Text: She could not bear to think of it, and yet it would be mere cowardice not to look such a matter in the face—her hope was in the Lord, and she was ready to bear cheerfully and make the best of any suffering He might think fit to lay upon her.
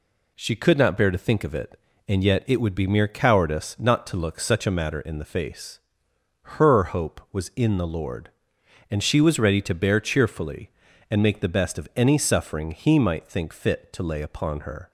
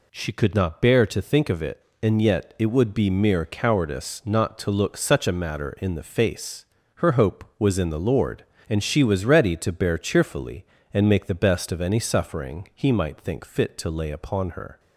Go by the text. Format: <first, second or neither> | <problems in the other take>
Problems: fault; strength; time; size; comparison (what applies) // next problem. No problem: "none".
neither | none